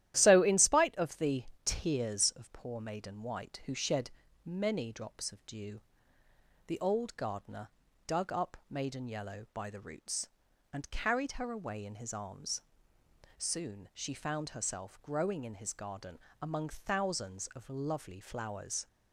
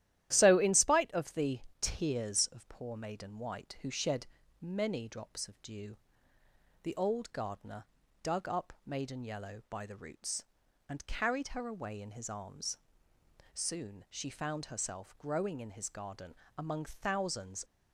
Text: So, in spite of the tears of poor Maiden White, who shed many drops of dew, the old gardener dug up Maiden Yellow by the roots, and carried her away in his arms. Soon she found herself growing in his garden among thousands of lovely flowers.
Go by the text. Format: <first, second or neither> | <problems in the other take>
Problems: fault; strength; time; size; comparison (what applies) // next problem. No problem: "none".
first | starts louder than the rest; strong; until 1.3 s; 12.5 dB; strong in the first // pauses between "the" and "tears"; slight; at 1.5 s; 0.22 s long; slight in the first // pauses between "shed" and "many"; slight; at 4.2 s; 0.34 s long; slight in the first // pauses between "gardener" and "dug"; at 7.8 s; 0.40 s long; also in the first // pauses between "garden" and "among"; slight; at 16.3 s; 0.24 s long; slight in the first // stops before "of lovely flowers"; at 17.6 s